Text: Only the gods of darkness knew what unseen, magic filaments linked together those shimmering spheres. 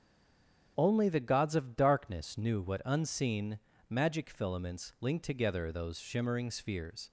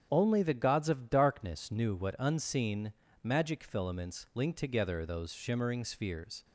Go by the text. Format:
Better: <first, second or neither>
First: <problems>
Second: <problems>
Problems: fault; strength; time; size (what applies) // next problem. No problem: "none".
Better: second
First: stays silent before the first word; slight; until 0.7 s; 0.7 s long // starts louder than the rest; strong; until 1.7 s; 8 dB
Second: starts louder than the rest; strong; until 1.1 s; 8 dB